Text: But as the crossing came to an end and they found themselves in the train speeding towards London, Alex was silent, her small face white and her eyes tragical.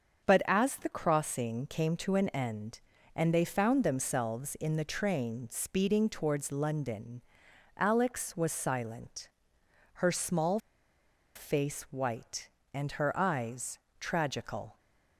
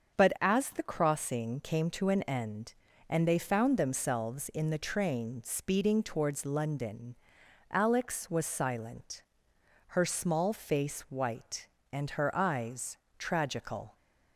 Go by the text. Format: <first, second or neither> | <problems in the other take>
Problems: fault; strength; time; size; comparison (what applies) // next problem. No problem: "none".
second | starts louder than the rest; until 1.2 s; 6.5 dB; also in the second // pauses between "small" and "face"; noticeable; at 10.5 s; 0.76 s long // pauses between "eyes" and "tragical"; slight; at 13.7 s; 0.22 s long; slight in the second